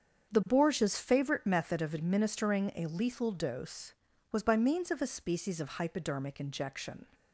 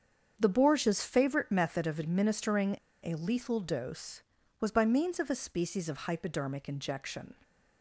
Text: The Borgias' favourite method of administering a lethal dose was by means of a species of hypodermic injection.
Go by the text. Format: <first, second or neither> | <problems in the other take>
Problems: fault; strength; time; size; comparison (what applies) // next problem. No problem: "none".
first | starts louder than the rest; strong; until 1.4 s; 7.5 dB; strong in the first // pauses between "administering" and "a"; slight; at 2.7 s; 0.27 s long